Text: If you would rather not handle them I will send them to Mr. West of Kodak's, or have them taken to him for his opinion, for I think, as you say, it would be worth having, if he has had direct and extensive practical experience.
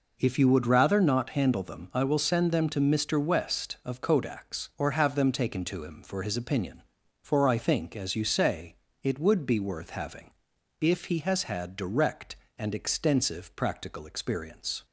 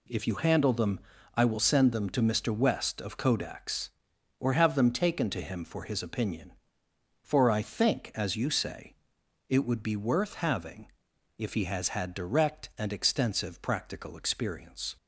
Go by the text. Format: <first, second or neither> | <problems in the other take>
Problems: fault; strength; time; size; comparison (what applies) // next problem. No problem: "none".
first | skips "would rather not"; at 0.3 s // pauses between "them" and "I"; slight; at 0.9 s; 0.36 s long